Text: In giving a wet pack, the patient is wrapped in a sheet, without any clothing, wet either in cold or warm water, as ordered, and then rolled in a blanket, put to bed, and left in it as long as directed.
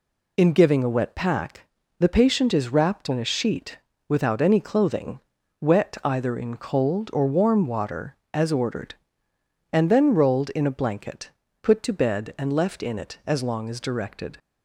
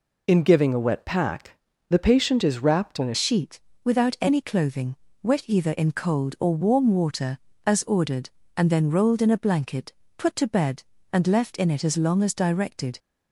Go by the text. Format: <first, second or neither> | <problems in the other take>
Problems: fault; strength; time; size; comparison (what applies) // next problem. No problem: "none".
first | changes voice at "sheet"; from 3.1 s on; 9.8 s long